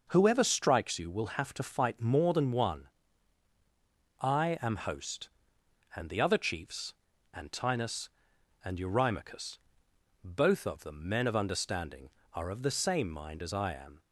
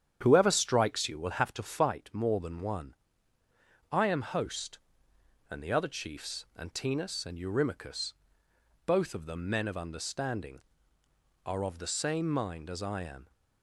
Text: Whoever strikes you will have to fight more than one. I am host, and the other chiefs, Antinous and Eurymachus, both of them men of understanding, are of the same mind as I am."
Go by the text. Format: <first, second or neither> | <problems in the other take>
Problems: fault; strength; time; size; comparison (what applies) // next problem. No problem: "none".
first | starts louder than the rest; strong; until 2.0 s; 9 dB